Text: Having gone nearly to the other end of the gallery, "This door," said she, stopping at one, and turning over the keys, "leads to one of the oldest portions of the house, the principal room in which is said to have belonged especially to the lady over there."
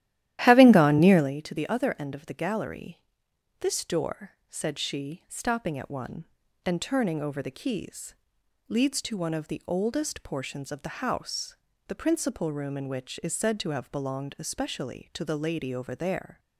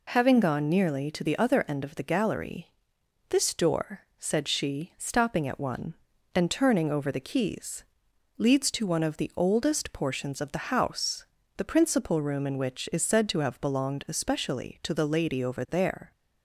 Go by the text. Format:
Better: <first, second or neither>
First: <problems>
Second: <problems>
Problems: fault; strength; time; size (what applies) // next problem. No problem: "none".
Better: second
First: starts louder than the rest; strong; until 1.3 s; 13 dB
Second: none